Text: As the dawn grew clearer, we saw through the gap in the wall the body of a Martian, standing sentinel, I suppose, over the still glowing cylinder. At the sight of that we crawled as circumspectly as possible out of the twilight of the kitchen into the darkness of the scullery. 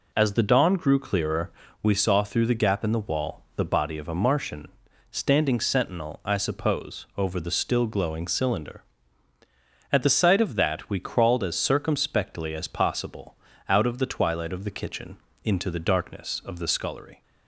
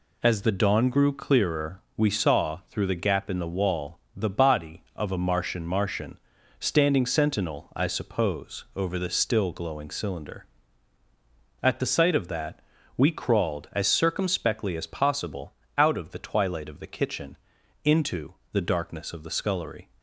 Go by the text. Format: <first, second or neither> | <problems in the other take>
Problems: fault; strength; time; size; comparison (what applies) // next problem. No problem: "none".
first | pauses between "wall" and "the"; slight; at 3.9 s; 0.16 s long // says "Martian" twice; at 5.6 s // pauses between "that" and "we"; slight; at 12.5 s; 0.36 s long // pauses between "possible" and "out"; slight; at 15.5 s; 0.22 s long; slight in the first // pauses between "kitchen" and "into"; noticeable; at 17.3 s; 0.48 s long; slight in the first // pauses between "into" and "the"; slight; at 18.3 s; 0.18 s long